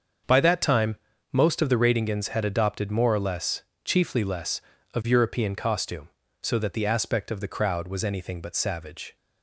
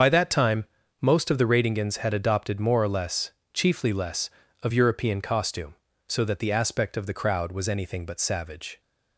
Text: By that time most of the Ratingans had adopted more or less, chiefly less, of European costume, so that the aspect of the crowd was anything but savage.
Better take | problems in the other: first | loses the start of "By"; at 0.0 s; 55 ms // starts louder than the rest; until 1.3 s; 6.5 dB; also in the first // pauses between "time" and "most"; slight; at 0.6 s; 0.36 s long; slight in the first

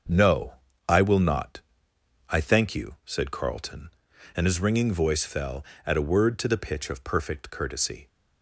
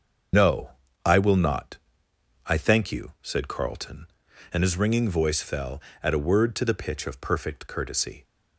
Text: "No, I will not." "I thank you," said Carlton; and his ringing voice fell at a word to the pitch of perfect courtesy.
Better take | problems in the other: first | loses the start of "No"; at 0.3 s; 105 ms // starts louder than the rest; until 1.6 s; 7 dB; also in the first

